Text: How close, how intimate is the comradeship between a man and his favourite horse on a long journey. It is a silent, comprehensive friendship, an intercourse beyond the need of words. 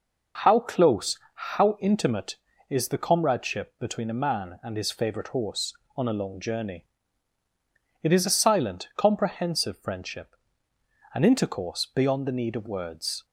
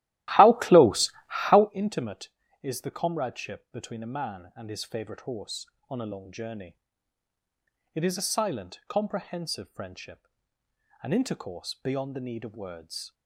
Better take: first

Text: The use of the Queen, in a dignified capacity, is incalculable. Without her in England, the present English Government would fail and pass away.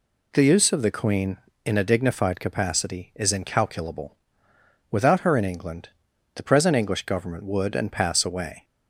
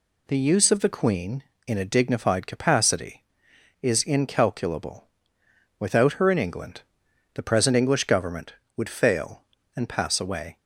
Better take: second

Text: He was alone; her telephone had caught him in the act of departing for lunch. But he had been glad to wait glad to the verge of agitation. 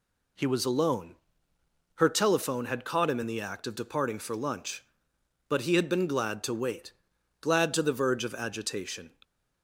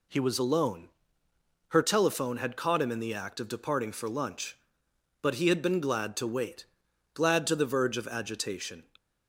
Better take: neither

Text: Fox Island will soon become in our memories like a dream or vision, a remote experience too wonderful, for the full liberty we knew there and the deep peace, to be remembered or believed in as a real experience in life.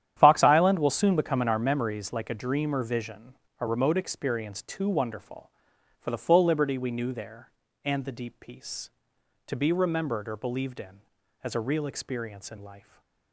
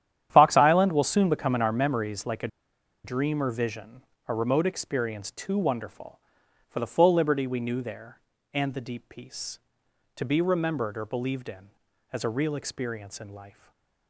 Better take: first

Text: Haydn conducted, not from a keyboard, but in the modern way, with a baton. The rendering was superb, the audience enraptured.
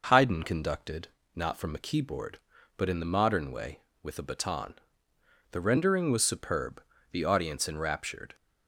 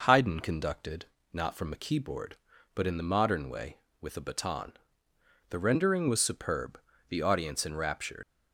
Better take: first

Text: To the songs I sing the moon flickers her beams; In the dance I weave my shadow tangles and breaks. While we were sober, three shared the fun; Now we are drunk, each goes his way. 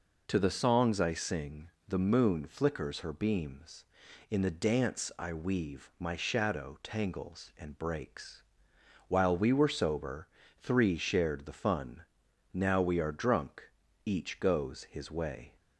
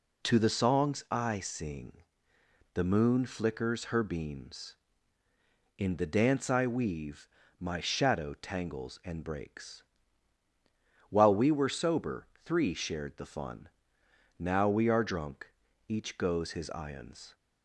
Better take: first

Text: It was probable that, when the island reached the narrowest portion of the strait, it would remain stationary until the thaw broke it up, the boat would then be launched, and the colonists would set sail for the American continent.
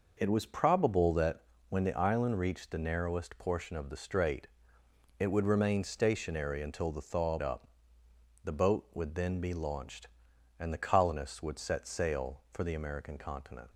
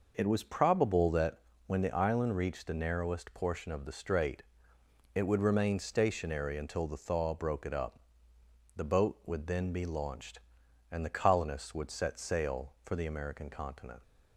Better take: second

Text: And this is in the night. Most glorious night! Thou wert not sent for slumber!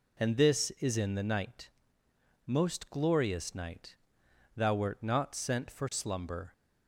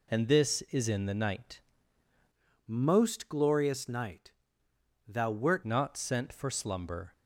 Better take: first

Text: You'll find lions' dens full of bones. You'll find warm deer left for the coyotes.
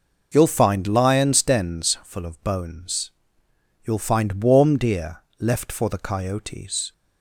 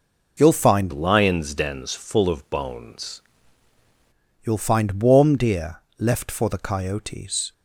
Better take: first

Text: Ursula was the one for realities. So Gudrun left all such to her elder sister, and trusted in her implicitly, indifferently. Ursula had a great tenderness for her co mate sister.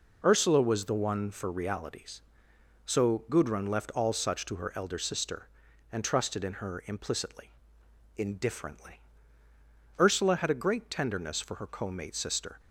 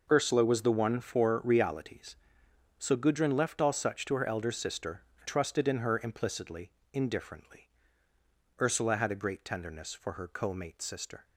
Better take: first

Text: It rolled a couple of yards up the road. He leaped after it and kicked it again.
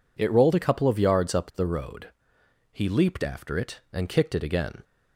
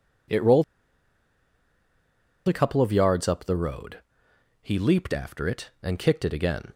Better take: first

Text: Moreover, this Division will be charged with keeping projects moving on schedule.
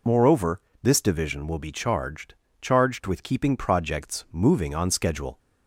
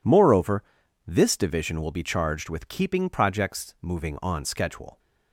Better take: second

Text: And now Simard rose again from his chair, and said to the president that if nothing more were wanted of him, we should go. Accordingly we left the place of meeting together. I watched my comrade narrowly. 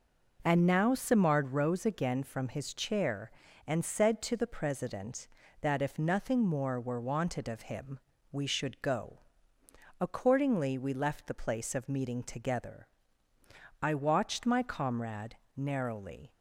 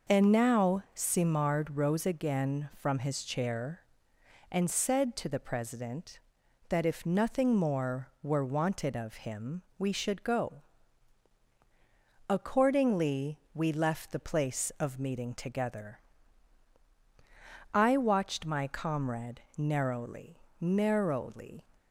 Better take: first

